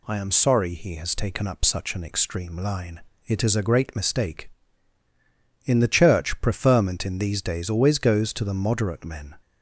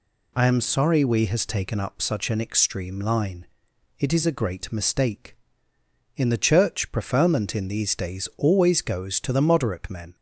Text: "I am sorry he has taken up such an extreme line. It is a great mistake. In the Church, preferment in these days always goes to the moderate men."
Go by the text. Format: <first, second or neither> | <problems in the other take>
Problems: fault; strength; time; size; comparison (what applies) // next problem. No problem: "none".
first | says "we" for "he"; at 1.0 s